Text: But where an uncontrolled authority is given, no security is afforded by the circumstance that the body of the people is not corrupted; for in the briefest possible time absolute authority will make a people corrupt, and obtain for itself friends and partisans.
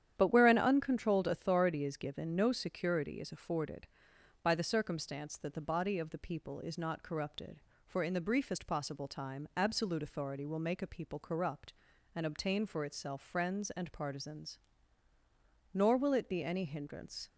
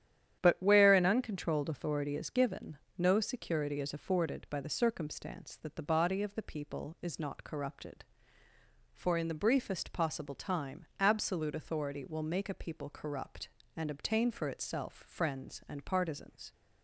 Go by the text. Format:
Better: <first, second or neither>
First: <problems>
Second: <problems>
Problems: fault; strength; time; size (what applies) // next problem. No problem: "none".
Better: second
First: starts louder than the rest; strong; until 1.1 s; 10 dB // goes on to say "Nor will it be any hindrance"; from 15.7 s on; 1.5 s long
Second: starts louder than the rest; strong; until 1.4 s; 10 dB